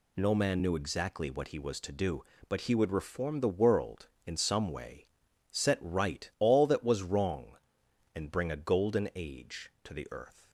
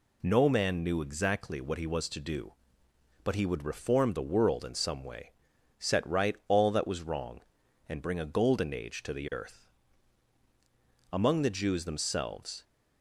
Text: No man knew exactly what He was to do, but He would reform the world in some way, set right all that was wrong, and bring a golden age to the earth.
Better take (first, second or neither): first